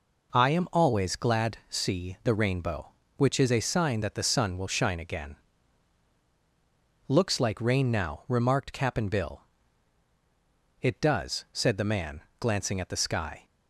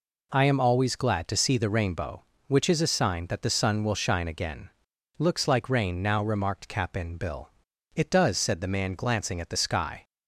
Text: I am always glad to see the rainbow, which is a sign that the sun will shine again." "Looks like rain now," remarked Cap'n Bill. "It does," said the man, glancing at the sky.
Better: second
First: skips "to"; at 1.6 s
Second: none

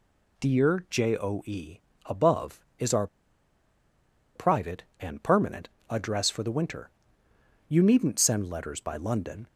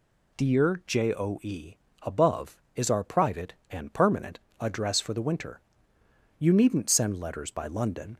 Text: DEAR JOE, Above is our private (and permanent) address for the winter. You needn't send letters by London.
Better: second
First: pauses between "our" and "private"; strong; at 3.0 s; 1.2 s long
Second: none

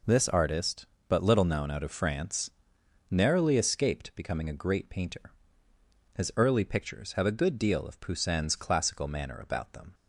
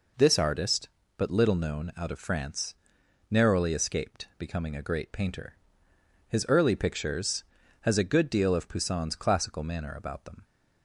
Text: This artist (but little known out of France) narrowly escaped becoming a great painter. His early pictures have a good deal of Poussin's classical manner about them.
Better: first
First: none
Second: says "has" for "have"; at 7.7 s

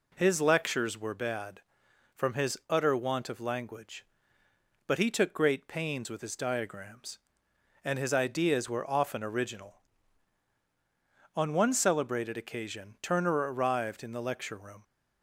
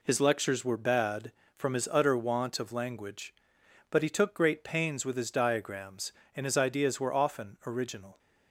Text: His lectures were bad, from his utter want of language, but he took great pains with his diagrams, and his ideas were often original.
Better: second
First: goes on to say "On one celebrated occasion Turner arrived in the lecture room"; strong; from 11.3 s on; 3.4 s long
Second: none

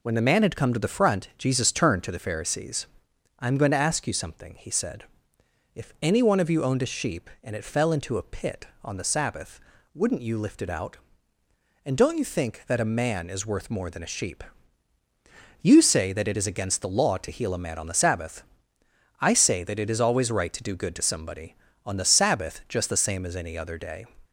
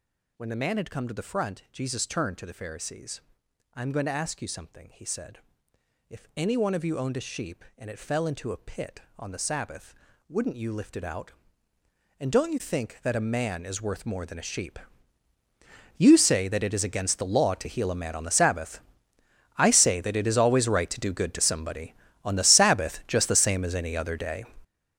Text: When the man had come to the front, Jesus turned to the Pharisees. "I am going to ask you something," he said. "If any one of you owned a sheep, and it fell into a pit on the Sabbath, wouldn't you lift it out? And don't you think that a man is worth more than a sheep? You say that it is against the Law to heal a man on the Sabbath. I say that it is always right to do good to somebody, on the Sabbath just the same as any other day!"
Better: first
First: none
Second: gets louder; strong; throughout; 12 dB

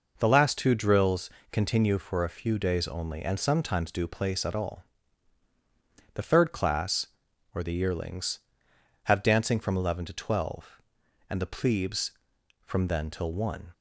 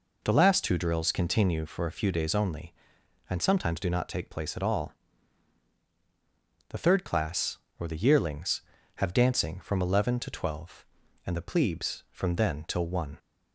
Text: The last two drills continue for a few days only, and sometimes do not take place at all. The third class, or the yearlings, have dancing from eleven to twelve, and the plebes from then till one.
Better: second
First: pauses between "drills" and "continue"; slight; at 1.2 s; 0.22 s long // skips "not take"; at 4.0 s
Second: none

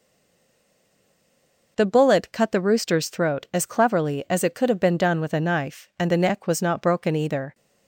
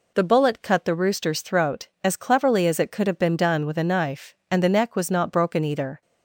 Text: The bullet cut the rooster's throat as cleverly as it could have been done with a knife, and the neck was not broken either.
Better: second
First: stays silent before the first word; noticeable; until 1.7 s; 1.7 s long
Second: none

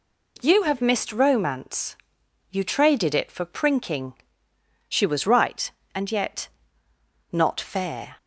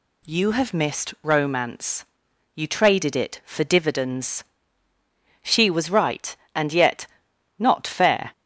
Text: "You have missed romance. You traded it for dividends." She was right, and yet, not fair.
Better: second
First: says "prinking" for "dividends"; at 3.4 s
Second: none

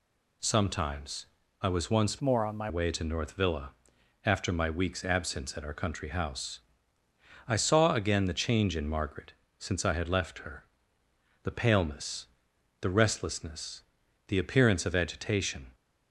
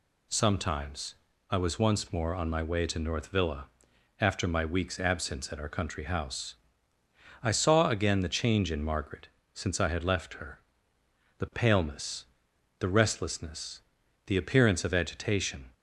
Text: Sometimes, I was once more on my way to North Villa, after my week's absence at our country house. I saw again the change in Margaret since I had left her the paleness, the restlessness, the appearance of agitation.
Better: second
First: changes voice from "more" to "my"; from 2.2 to 2.6 s; 0.4 s long // pauses between "Margaret" and "since"; slight; at 9.3 s; 0.26 s long // pauses between "her" and "the"; noticeable; at 10.6 s; 0.78 s long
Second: pauses between "Margaret" and "since"; slight; at 9.2 s; 0.26 s long // pauses between "her" and "the"; noticeable; at 10.6 s; 0.78 s long

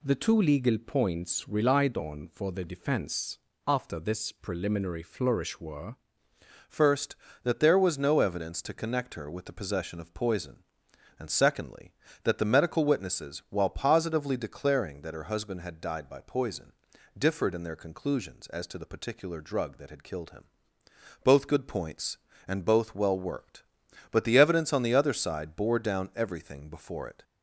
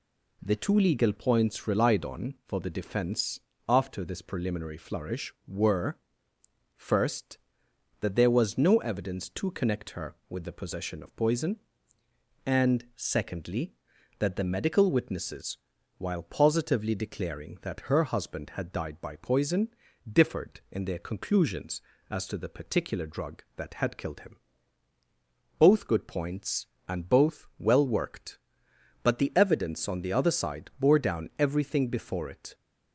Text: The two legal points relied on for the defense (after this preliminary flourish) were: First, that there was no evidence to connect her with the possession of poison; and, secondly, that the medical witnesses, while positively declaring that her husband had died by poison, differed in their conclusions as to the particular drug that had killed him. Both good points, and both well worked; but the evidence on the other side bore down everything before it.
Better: second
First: changes voice at "First"; from 6.6 s on; 20.6 s long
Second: none

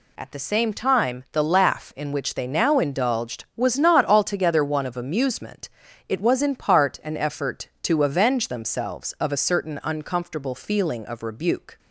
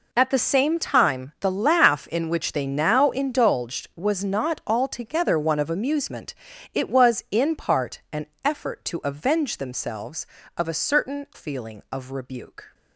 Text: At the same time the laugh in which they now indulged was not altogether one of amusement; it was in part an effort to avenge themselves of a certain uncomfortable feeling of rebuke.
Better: first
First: none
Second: pauses between "an" and "effort"; slight; at 8.2 s; 0.18 s long // skips "uncomfortable"; at 11.3 s

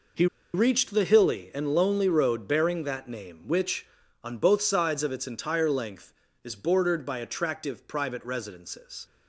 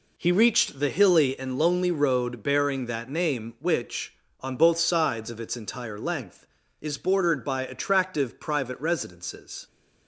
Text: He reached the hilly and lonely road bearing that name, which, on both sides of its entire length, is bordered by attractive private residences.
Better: second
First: pauses between "He" and "reached"; slight; at 0.2 s; 0.28 s long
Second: none

